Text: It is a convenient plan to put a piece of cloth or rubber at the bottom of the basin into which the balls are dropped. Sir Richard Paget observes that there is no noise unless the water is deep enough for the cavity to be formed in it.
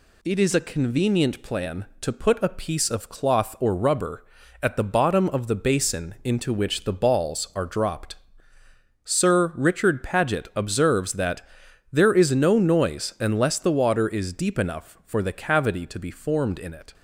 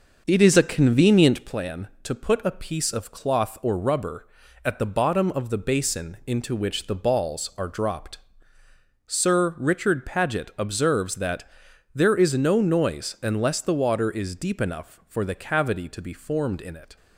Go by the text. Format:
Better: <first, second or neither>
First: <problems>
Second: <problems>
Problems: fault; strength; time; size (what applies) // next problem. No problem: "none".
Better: first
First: pauses between "that" and "there"; noticeable; at 11.4 s; 0.50 s long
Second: starts louder than the rest; noticeable; until 1.6 s; 6 dB // pauses between "that" and "there"; noticeable; at 11.4 s; 0.50 s long